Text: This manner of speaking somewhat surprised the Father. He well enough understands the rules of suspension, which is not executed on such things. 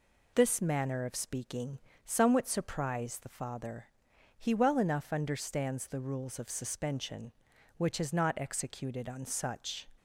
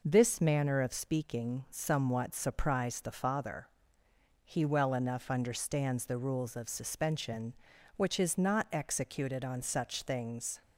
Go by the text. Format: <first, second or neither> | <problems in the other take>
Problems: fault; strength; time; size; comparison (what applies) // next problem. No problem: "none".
second | pauses between "speaking" and "somewhat"; slight; at 1.7 s; 0.26 s long // stops before "things"; at 9.9 s